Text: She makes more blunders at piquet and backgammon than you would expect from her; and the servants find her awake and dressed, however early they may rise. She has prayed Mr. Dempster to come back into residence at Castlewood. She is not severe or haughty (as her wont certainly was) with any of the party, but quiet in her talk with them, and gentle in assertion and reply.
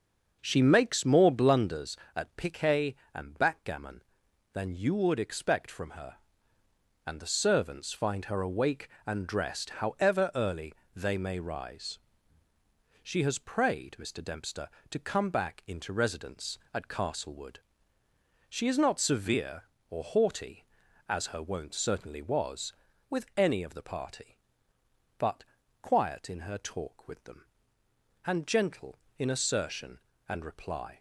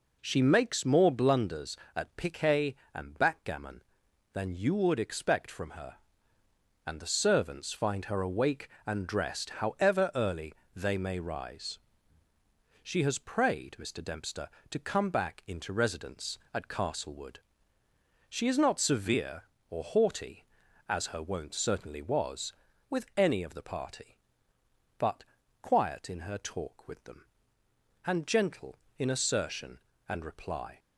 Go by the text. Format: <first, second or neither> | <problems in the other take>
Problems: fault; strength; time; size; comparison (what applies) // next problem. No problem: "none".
second | starts louder than the rest; until 2.0 s; 6.5 dB // pauses between "early" and "they"; slight; at 10.7 s; 0.22 s long; slight in the second // pauses between "but" and "quiet"; at 25.4 s; 0.40 s long; also in the second